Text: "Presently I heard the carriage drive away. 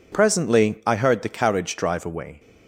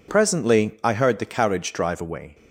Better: neither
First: none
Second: none

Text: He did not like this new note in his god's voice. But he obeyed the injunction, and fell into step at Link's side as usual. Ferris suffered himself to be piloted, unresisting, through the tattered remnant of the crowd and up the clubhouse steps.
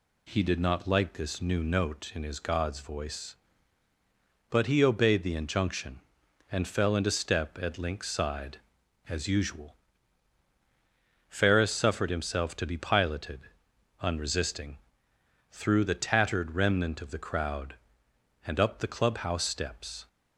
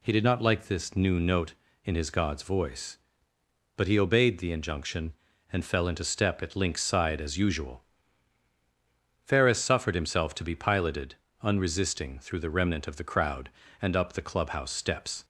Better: first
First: none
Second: skips "tattered"; at 12.5 s

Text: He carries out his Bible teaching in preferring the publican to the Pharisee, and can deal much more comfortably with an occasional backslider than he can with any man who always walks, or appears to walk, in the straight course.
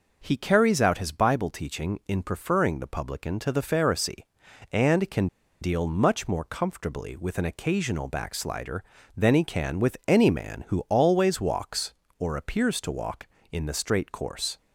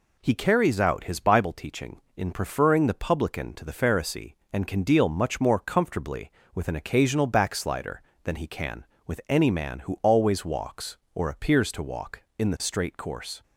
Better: second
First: pauses between "can" and "deal"; slight; at 5.2 s; 0.34 s long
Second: none

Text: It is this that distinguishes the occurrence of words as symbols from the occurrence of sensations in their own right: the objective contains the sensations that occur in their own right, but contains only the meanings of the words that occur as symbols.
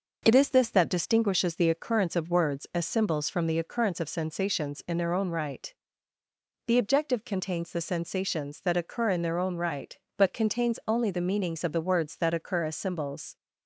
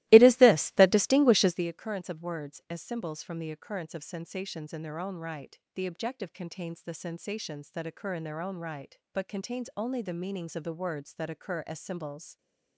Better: first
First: none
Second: starts louder than the rest; strong; until 1.6 s; 18 dB

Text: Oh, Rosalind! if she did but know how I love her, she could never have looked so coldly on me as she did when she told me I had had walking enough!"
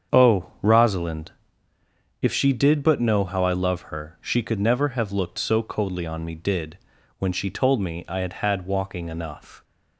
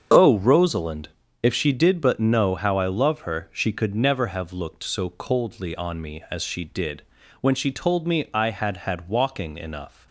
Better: second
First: starts louder than the rest; strong; until 1.2 s; 7.5 dB // skips "as she"; at 6.3 s // pauses between "did" and "when"; at 6.7 s; 0.42 s long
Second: starts louder than the rest; until 1.4 s; 7 dB // pauses between "did" and "when"; at 7.0 s; 0.40 s long

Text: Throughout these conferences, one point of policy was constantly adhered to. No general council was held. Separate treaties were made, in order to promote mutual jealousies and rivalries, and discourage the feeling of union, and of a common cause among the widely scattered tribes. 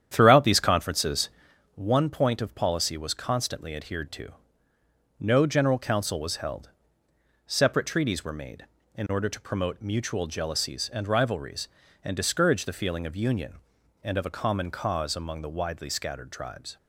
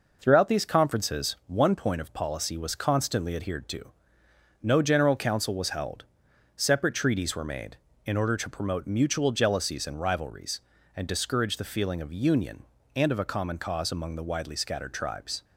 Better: second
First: starts louder than the rest; strong; until 1.7 s; 9.5 dB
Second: none

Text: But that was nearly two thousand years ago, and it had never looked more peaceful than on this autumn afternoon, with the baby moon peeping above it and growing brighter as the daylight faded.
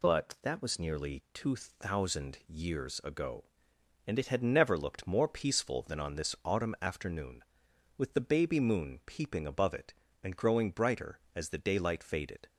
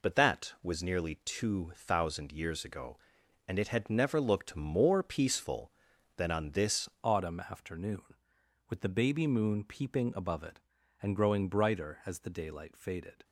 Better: first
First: none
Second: changes voice at "autumn"; from 7.0 s on; 6.2 s long

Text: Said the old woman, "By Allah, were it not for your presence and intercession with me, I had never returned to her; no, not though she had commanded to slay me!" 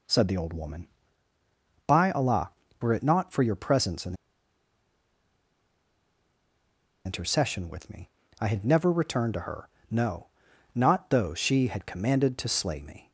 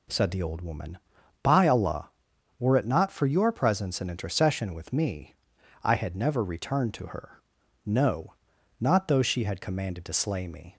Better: second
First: pauses between "and" and "intercession"; strong; at 4.1 s; 2.9 s long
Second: none

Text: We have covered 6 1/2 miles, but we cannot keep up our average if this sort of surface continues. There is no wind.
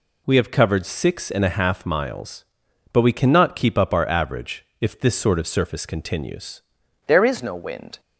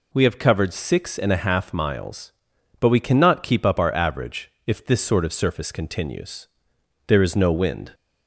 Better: second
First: pauses between "average" and "if"; slight; at 4.6 s; 0.16 s long // changes voice at "There"; from 7.0 s on; 0.9 s long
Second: pauses between "average" and "if"; slight; at 4.4 s; 0.16 s long

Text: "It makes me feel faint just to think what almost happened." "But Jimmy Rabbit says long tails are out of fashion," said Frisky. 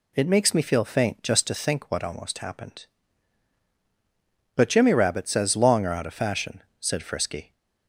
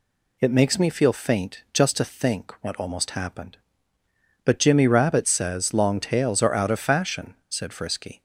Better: second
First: skips "tails"; at 5.8 s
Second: none

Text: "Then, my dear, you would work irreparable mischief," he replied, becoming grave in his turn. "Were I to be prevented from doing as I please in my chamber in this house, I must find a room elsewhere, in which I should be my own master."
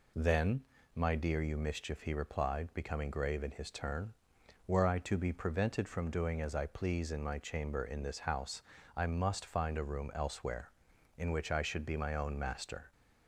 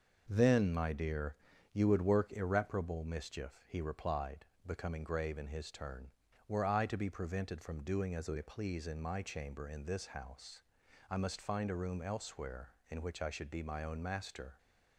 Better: second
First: skips "would work irreparable"; at 1.5 s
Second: none

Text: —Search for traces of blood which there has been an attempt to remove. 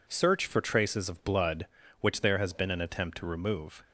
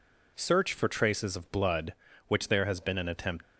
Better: first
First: none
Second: stops before "to remove"; at 3.4 s

